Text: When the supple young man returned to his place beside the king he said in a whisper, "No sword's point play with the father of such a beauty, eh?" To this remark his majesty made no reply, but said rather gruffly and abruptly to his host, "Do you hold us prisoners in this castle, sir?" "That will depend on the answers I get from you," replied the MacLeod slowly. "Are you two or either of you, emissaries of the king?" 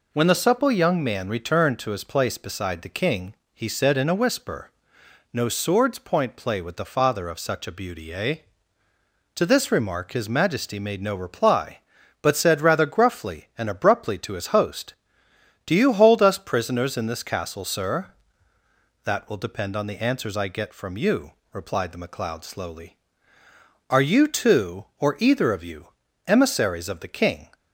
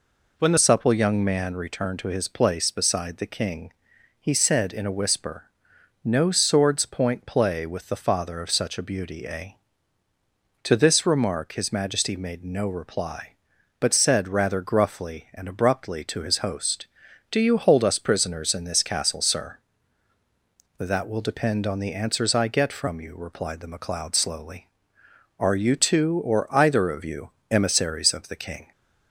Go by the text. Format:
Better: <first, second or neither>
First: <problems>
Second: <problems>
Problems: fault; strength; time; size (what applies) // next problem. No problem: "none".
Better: first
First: pauses between "king" and "he"; slight; at 3.3 s; 0.20 s long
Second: changes voice at "supple"; from 0.5 s on; 28.2 s long // pauses between "king" and "he"; noticeable; at 3.7 s; 0.48 s long